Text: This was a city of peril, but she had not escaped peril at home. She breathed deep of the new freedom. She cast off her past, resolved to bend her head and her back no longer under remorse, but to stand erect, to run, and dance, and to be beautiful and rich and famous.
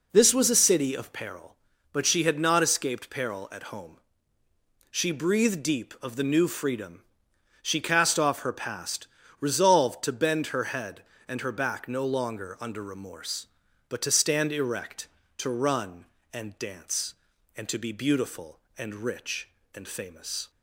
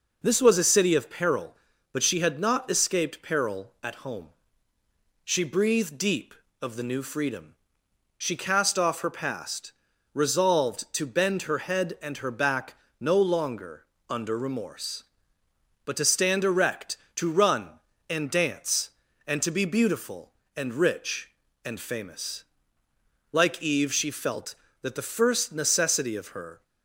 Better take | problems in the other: first | pauses between "back" and "no"; slight; at 12.7 s; 0.26 s long // pauses between "longer" and "under"; slight; at 13.8 s; 0.26 s long // goes on to say "Like Eve she felt that the first necessity of her"; strong; from 23.3 s on; 3.3 s long

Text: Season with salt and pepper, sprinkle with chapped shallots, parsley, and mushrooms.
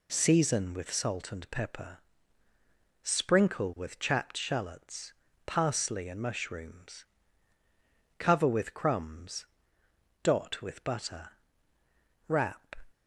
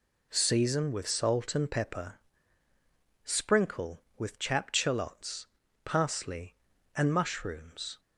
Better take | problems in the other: second | goes on to say "Cover with crumbs dot with butter wrap"; strong; from 8.1 s on; 4.5 s long

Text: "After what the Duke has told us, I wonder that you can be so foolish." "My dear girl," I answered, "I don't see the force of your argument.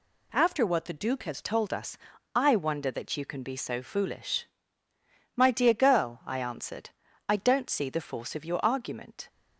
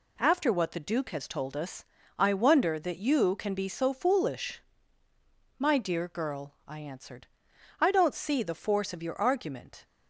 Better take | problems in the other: second | changes voice at "told"; from 1.4 s on; 7.8 s long

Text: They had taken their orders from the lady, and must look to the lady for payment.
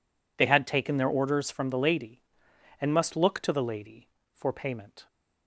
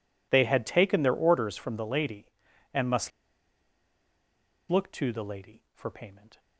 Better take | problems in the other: first | pauses between "must" and "look"; strong; at 3.1 s; 1.6 s long

